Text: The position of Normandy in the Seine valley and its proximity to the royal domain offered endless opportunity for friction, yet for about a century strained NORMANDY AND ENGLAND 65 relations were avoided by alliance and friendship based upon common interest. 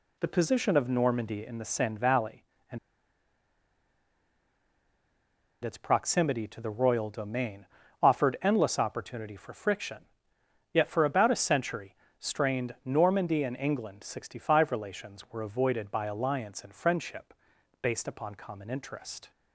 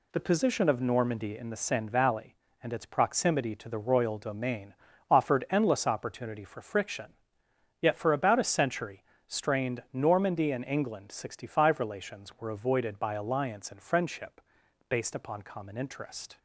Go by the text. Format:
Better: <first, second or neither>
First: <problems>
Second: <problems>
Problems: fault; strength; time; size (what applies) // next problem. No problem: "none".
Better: second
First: pauses between "and" and "its"; strong; at 2.7 s; 2.8 s long // pauses between "domain" and "offered"; at 7.6 s; 0.38 s long // pauses between "century" and "strained"; slight; at 11.9 s; 0.24 s long // pauses between "friendship" and "based"; noticeable; at 17.3 s; 0.48 s long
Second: pauses between "domain" and "offered"; at 4.7 s; 0.38 s long // pauses between "century" and "strained"; slight; at 9.0 s; 0.24 s long // pauses between "friendship" and "based"; noticeable; at 14.4 s; 0.48 s long